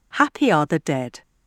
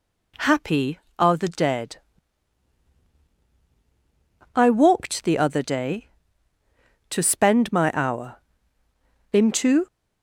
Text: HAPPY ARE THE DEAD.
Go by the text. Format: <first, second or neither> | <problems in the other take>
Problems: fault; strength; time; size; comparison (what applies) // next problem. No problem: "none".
first | goes on to say "I walked the other day to spend my hour Into"; strong; from 4.5 s on; 5.3 s long